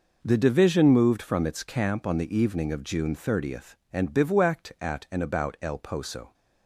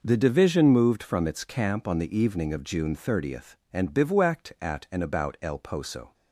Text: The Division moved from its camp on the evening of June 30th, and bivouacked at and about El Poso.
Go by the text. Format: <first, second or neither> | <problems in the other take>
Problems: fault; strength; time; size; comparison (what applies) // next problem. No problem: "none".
neither | none